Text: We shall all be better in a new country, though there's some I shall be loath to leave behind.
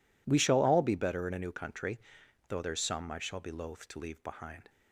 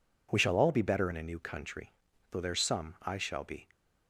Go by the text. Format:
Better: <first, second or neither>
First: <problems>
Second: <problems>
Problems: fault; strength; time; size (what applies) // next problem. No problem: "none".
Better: first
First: none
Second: stops before "loath to leave behind"; at 3.7 s